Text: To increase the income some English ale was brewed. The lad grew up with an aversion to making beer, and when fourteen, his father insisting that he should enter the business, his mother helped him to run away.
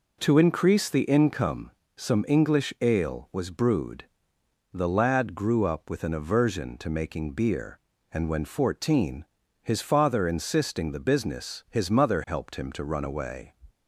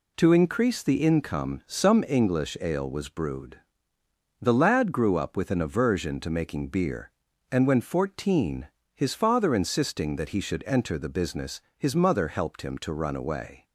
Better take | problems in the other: second | pauses between "income" and "some"; slight; at 1.7 s; 0.24 s long // skips "that he should enter"; at 10.9 s

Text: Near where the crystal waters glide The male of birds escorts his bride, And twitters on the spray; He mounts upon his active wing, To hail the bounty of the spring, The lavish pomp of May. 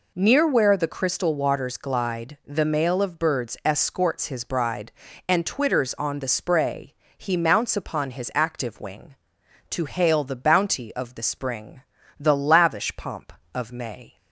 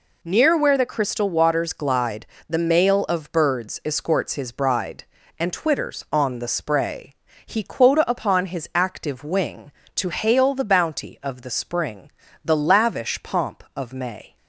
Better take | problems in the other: first | pauses between "glide" and "The"; slight; at 2.2 s; 0.20 s long // says "quota" for "mounts"; at 7.6 s

